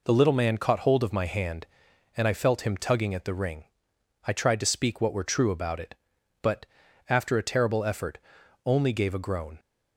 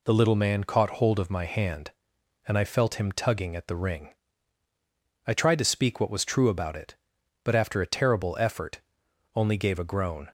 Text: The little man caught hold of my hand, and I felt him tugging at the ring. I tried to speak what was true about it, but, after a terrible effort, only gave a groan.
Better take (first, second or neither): second